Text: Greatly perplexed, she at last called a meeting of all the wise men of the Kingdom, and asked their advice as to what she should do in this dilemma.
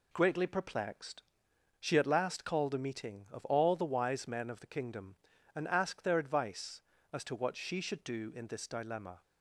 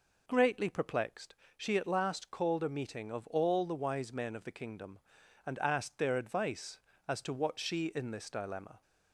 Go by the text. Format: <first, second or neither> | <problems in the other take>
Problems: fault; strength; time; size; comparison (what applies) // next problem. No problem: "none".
first | skips "should do"; at 7.9 s